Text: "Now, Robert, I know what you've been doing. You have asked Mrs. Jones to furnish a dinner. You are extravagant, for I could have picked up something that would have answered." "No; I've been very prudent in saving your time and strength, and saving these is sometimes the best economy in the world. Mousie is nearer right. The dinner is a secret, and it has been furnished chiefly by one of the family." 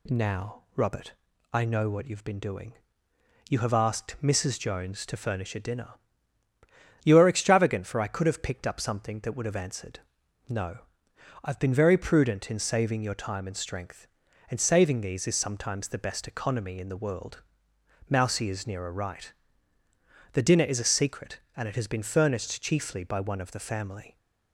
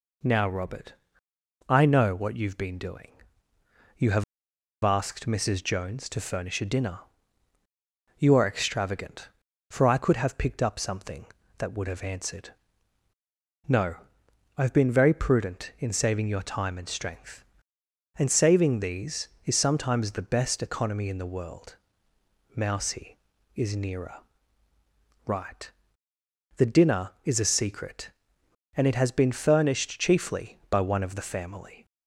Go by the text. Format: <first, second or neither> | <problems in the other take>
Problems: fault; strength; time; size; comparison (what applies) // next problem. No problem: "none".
first | pauses between "have" and "asked"; noticeable; at 4.2 s; 0.61 s long // pauses between "nearer" and "right"; at 24.2 s; 1.0 s long